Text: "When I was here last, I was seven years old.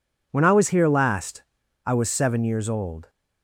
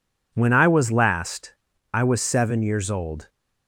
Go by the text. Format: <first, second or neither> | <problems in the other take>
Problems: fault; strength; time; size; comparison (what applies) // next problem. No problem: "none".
first | skips "here"; at 0.9 s